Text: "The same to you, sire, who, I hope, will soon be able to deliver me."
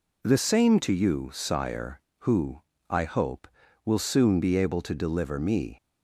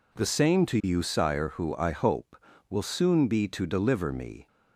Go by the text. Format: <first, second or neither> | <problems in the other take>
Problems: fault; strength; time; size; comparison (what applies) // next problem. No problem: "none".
first | skips "able"; at 3.4 s